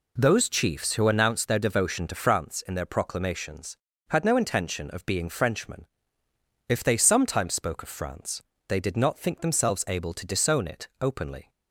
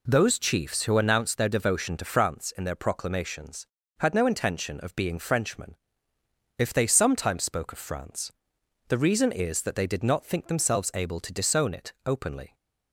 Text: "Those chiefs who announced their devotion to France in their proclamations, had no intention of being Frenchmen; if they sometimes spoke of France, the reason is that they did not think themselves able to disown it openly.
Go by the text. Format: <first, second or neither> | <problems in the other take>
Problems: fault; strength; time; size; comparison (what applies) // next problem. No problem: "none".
second | skips "the reason is that"; at 8.5 s